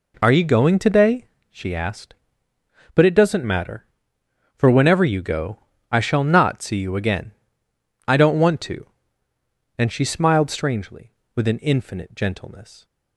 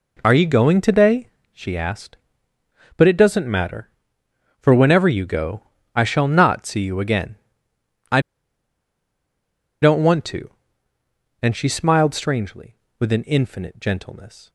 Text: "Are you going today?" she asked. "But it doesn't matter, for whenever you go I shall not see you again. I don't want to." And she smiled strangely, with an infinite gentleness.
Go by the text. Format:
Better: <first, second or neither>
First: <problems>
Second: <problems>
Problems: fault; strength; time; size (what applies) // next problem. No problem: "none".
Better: first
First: pauses between "go" and "I"; slight; at 5.5 s; 0.32 s long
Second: pauses between "go" and "I"; slight; at 5.6 s; 0.32 s long // pauses between "I" and "don't"; strong; at 8.1 s; 1.6 s long